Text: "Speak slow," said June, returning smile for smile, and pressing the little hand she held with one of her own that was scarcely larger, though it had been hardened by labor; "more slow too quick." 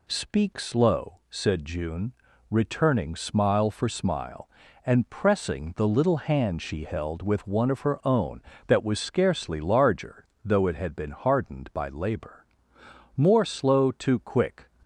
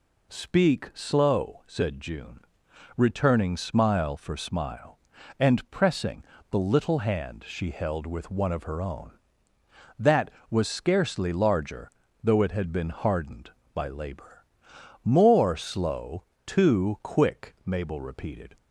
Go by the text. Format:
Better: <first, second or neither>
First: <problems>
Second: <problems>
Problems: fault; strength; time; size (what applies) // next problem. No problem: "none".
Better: first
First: none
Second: pauses between "pressing" and "the"; slight; at 6.2 s; 0.28 s long // pauses between "slow" and "too"; slight; at 16.2 s; 0.22 s long // goes on to say "Mabel repeated"; noticeable; from 17.6 s on; 0.94 s long